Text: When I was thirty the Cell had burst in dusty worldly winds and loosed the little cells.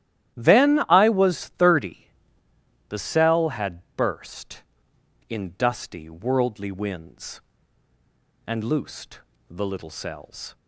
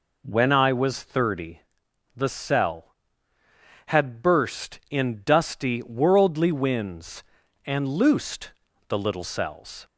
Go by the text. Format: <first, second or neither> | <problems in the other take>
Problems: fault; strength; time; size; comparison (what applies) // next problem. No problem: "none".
second | starts louder than the rest; strong; until 1.4 s; 12.5 dB // says "Then" for "When"; at 0.3 s // pauses between "thirty" and "the"; noticeable; at 2.0 s; 0.82 s long; noticeable in the second // pauses between "had" and "burst"; slight; at 3.8 s; 0.16 s long // pauses between "loosed" and "the"; slight; at 9.1 s; 0.28 s long; slight in the second